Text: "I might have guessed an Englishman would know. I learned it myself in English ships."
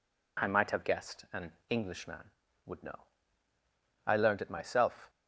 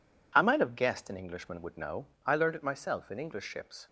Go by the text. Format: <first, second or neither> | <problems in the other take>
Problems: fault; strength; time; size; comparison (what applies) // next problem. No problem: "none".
second | pauses between "an" and "Englishman"; slight; at 1.5 s; 0.16 s long // stops before "in English ships"; at 5.0 s